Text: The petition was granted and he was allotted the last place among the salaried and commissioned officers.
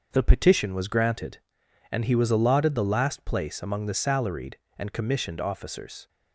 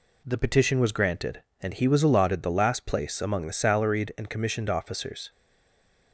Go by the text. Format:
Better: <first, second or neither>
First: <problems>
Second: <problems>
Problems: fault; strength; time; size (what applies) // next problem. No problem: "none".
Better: first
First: none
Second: stays silent after the last word; slight; from 5.3 s on; 0.8 s long